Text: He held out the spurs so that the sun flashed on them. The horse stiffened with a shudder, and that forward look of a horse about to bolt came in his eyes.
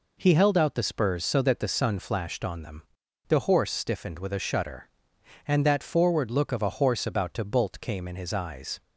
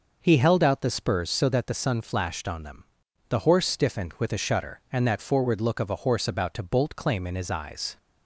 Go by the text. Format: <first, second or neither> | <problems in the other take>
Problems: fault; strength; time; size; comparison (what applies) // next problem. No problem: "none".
first | says "claim" for "came"; at 6.9 s